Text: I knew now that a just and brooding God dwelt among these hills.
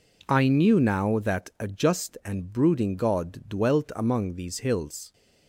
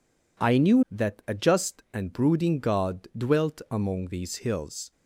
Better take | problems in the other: first | skips "now"; at 0.8 s

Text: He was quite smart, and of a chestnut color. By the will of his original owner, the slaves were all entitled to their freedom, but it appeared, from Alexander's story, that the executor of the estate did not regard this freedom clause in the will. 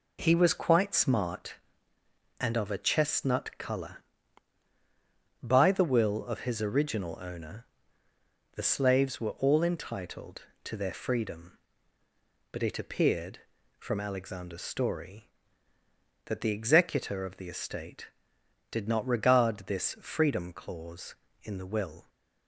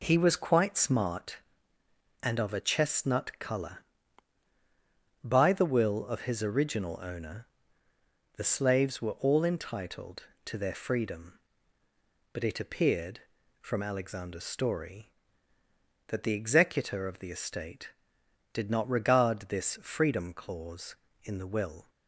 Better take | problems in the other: neither | none

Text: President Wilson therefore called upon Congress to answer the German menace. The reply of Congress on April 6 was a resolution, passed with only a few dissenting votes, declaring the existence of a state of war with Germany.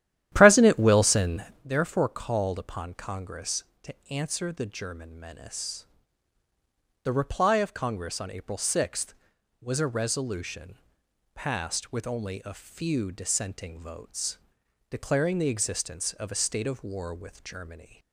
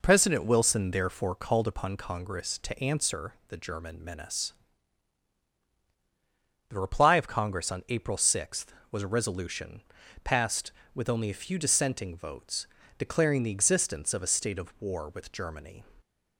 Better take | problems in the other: second | starts louder than the rest; strong; until 1.7 s; 12 dB // pauses between "Wilson" and "therefore"; slight; at 1.4 s; 0.20 s long // pauses between "to" and "answer"; slight; at 3.9 s; 0.16 s long

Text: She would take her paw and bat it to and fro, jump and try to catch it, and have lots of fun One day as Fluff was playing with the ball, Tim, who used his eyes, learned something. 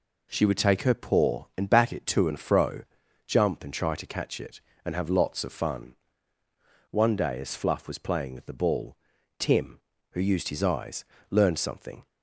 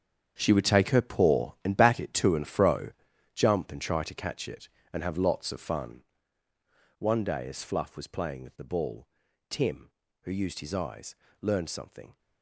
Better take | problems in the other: first | gets quieter; strong; throughout; 13.5 dB // pauses between "fun" and "One"; noticeable; at 6.0 s; 0.98 s long; noticeable in the first

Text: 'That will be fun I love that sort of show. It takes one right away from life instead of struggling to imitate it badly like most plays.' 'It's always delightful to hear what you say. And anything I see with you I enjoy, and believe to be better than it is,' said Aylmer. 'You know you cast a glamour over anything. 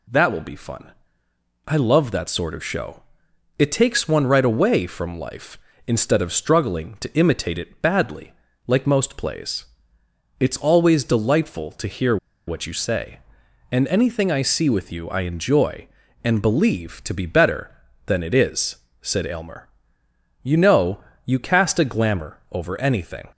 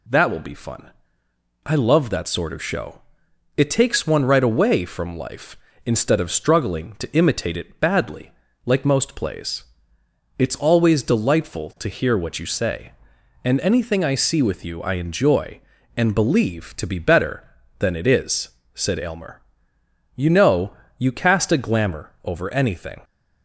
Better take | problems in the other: second | pauses between "fun" and "I"; noticeable; at 0.9 s; 0.74 s long; noticeable in the second // pauses between "badly" and "like"; slight; at 8.3 s; 0.34 s long; slight in the second // pauses between "hear" and "what"; slight; at 12.1 s; 0.30 s long // pauses between "know" and "you"; slight; at 21.0 s; 0.24 s long; slight in the second

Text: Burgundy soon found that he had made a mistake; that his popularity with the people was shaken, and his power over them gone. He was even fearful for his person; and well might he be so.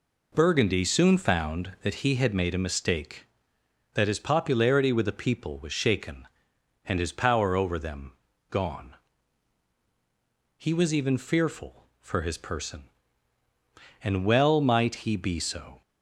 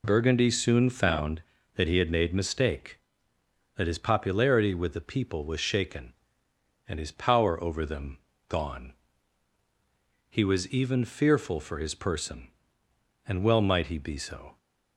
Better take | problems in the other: first | skips "a"; at 2.3 s // pauses between "them" and "gone"; slight; at 8.1 s; 0.28 s long; slight in the first

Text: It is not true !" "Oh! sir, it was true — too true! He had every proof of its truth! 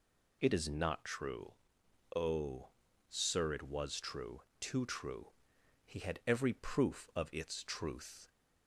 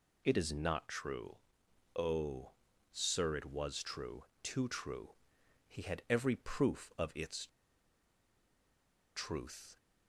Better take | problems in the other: first | pauses between "its" and "truth"; strong; at 7.4 s; 1.6 s long

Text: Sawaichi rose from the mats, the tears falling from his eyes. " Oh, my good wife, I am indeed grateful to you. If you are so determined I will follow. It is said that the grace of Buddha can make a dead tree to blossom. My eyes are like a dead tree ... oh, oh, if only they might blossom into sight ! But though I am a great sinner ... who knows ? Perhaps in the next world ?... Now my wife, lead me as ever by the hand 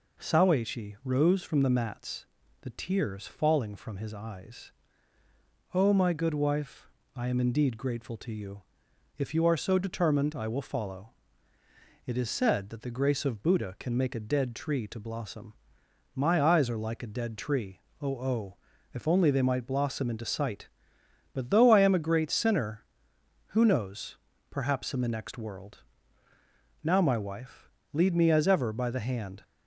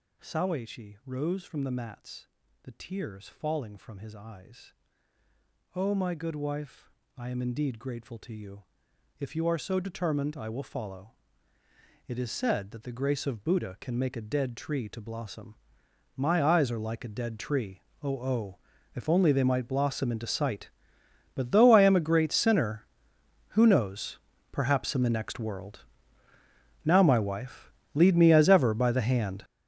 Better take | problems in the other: first | gets louder; strong; throughout; 15.5 dB

